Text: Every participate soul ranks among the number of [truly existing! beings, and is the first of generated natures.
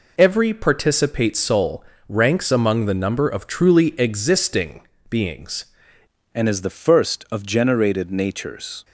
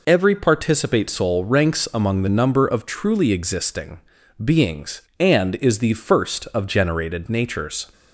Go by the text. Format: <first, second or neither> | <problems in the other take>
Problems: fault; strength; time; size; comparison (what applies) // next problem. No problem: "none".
second | pauses between "soul" and "ranks"; slight; at 1.8 s; 0.24 s long // changes voice at "and"; from 6.3 s on; 2.5 s long